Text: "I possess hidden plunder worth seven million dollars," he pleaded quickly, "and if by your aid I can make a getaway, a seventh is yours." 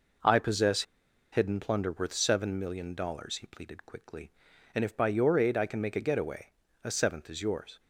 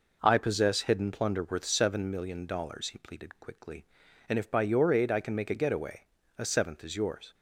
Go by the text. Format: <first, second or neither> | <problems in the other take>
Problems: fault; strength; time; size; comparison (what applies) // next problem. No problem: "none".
second | pauses between "possess" and "hidden"; noticeable; at 0.8 s; 0.49 s long